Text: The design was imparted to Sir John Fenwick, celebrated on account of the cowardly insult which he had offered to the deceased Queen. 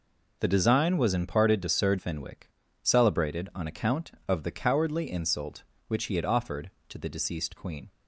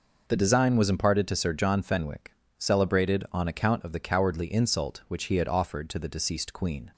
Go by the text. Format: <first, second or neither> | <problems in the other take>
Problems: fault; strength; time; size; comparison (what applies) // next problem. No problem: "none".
second | skips "John"; at 1.9 s